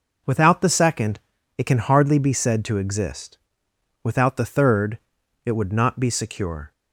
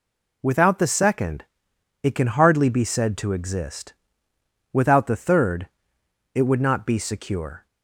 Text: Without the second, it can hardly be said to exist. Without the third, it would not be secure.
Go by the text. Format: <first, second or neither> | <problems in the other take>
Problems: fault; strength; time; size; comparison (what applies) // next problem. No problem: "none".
neither | none